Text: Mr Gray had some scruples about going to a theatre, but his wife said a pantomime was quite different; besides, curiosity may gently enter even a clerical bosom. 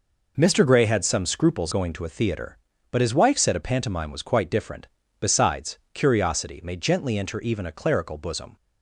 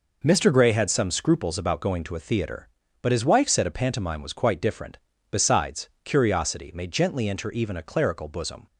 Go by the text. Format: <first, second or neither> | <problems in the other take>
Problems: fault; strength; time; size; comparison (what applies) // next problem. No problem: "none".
second | skips "about"; at 1.7 s